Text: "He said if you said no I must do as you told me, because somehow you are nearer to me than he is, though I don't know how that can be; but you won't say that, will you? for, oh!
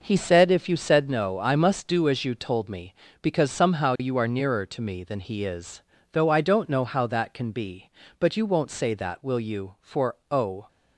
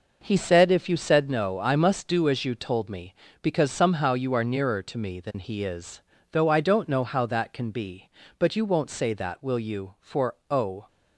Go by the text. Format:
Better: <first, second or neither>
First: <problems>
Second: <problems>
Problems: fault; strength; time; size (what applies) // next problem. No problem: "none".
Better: neither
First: none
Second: none